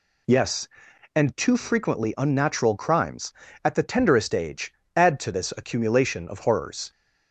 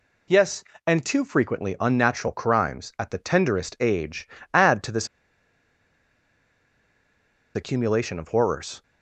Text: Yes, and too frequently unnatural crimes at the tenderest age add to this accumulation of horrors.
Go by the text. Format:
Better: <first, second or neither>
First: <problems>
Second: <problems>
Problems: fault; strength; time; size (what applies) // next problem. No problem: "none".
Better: first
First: pauses between "age" and "add"; slight; at 4.7 s; 0.20 s long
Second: pauses between "age" and "add"; slight; at 4.2 s; 0.24 s long // pauses between "this" and "accumulation"; strong; at 5.0 s; 2.4 s long